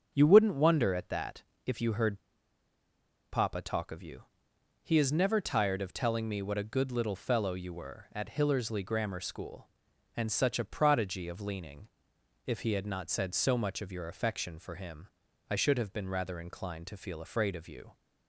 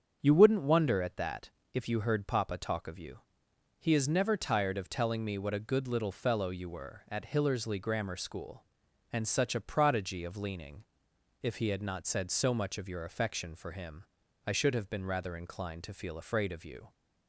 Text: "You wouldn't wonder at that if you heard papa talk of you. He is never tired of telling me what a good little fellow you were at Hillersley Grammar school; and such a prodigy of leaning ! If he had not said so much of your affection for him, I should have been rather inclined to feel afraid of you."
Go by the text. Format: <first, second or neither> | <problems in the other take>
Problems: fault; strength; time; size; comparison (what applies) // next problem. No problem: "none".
second | starts louder than the rest; strong; until 1.1 s; 7.5 dB; strong in the second // pauses between "that" and "if"; slight; at 1.4 s; 0.24 s long; slight in the second // pauses between "heard" and "papa"; at 2.1 s; 1.1 s long